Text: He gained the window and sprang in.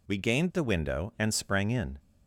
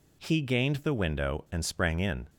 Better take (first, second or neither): second